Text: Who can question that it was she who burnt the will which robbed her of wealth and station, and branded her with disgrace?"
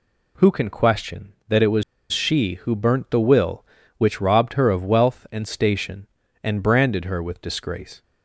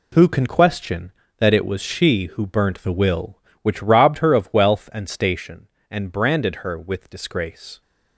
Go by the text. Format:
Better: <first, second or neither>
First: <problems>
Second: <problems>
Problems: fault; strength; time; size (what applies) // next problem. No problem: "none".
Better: second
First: pauses between "was" and "she"; slight; at 1.8 s; 0.29 s long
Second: none